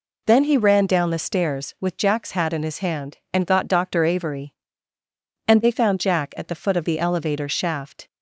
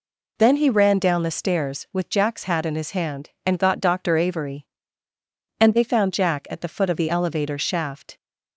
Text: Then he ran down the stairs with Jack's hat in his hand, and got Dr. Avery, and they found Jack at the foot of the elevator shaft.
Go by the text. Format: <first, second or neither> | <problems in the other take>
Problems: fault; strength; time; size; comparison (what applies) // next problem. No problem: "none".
neither | none